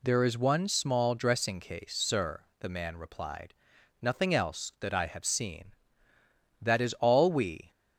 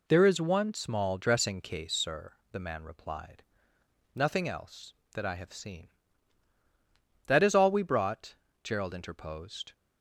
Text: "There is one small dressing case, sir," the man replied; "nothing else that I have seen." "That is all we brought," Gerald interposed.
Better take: second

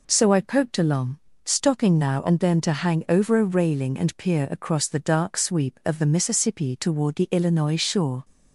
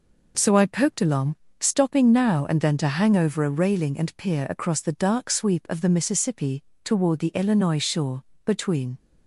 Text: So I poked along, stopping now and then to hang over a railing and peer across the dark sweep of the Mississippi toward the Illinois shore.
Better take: first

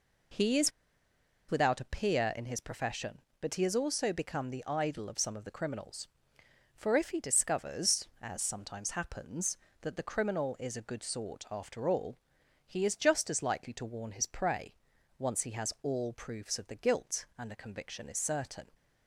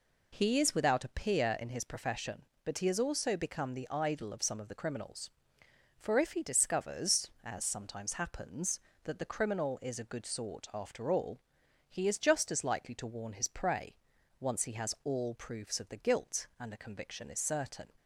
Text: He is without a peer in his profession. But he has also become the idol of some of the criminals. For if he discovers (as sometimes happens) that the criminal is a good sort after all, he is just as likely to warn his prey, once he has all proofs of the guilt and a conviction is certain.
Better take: second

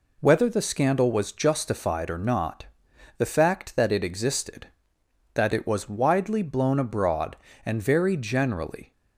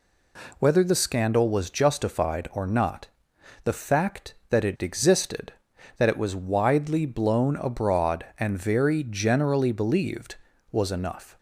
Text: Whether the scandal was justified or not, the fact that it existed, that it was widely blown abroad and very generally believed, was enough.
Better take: second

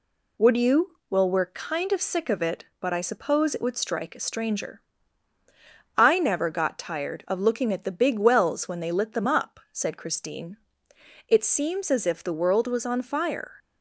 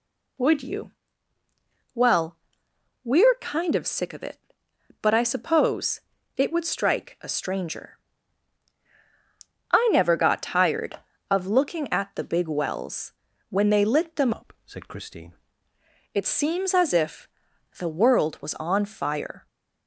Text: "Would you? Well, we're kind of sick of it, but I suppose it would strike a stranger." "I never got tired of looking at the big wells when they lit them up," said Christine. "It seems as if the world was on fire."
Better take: first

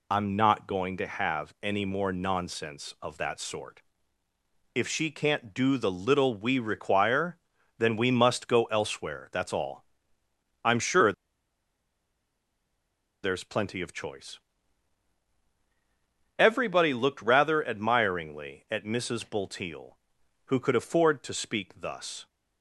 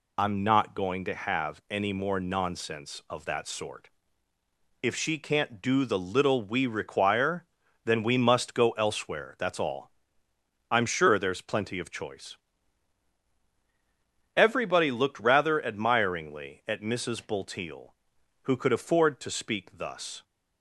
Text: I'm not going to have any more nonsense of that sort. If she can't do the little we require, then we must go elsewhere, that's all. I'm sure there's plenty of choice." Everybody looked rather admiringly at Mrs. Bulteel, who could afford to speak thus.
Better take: second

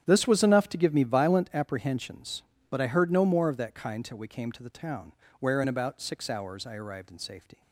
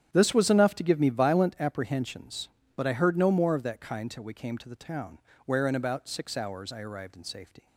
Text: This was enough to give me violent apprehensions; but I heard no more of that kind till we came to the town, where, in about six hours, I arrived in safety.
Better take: neither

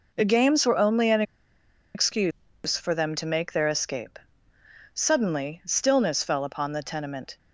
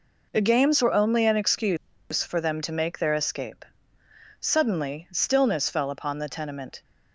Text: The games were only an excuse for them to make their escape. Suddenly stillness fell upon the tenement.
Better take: second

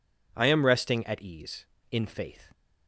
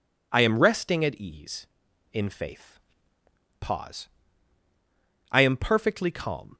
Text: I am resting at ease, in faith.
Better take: first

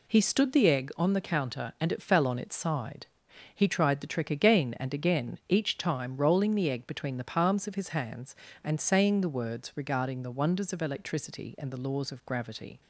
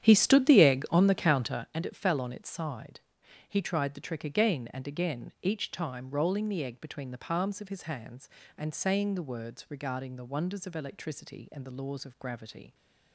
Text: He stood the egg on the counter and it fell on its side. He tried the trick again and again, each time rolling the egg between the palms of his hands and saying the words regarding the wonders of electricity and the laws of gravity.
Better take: first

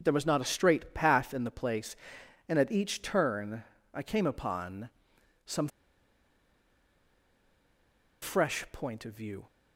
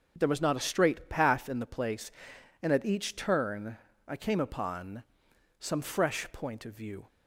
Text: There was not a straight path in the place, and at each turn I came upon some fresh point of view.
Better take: second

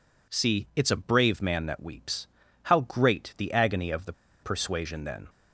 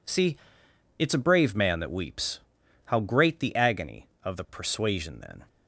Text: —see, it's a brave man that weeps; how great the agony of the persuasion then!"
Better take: second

